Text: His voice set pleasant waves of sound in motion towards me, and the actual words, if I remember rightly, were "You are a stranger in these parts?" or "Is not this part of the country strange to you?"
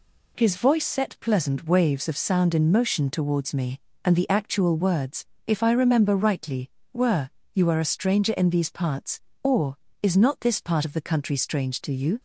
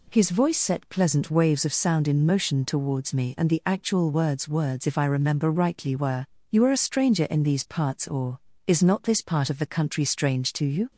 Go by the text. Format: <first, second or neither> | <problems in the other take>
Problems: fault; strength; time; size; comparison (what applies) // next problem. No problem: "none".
first | says "words" twice; at 4.4 s // pauses between "were" and "You"; slight; at 6.2 s; 0.24 s long; slight in the first